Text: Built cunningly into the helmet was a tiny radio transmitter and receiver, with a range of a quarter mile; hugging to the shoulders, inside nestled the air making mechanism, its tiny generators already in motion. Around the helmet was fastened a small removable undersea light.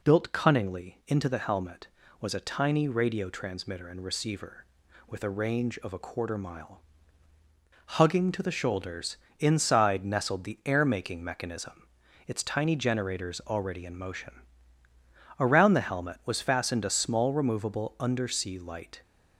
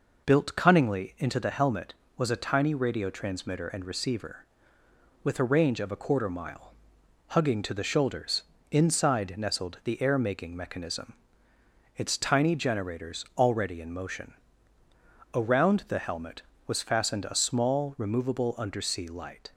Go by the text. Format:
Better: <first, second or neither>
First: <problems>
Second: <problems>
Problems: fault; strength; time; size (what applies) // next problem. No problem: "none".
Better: neither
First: none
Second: none